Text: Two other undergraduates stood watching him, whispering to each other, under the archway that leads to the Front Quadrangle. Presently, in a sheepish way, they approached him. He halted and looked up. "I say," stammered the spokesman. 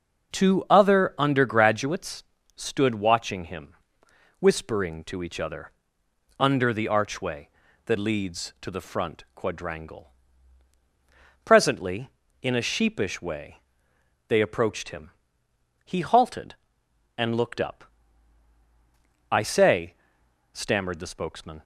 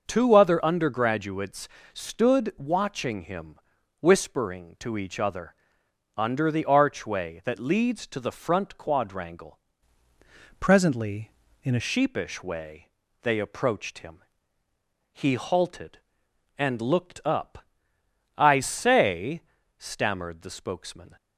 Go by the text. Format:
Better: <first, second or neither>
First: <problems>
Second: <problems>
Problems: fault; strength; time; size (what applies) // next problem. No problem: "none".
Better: first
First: starts louder than the rest; noticeable; until 1.4 s; 6 dB // pauses between "undergraduates" and "stood"; slight; at 2.2 s; 0.32 s long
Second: starts louder than the rest; until 1.0 s; 6.5 dB // pauses between "undergraduates" and "stood"; slight; at 1.6 s; 0.24 s long // changes voice from "Presently" to "a"; from 10.6 to 11.8 s; 1.2 s long